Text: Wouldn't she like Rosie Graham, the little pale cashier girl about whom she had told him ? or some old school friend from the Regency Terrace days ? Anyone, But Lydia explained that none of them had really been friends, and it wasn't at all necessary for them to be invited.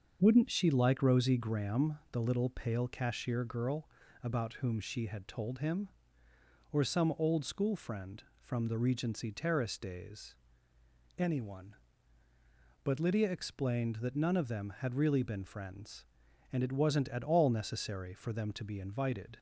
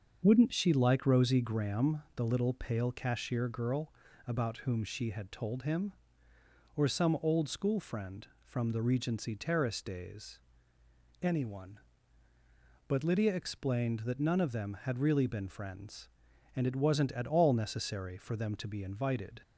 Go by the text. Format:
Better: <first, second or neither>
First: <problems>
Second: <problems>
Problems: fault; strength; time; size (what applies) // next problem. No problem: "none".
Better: neither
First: starts louder than the rest; until 1.2 s; 6.5 dB // pauses between "girl" and "about"; slight; at 3.8 s; 0.34 s long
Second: starts louder than the rest; until 1.2 s; 6.5 dB // pauses between "girl" and "about"; slight; at 3.9 s; 0.34 s long